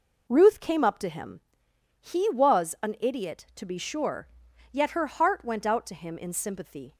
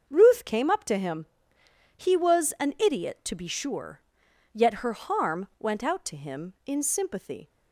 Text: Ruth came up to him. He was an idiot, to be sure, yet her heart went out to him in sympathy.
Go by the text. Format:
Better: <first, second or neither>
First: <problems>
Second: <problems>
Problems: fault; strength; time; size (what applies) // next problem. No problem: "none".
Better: first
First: none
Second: starts louder than the rest; until 1.0 s; 6.5 dB // says "harm" for "heart"; at 4.9 s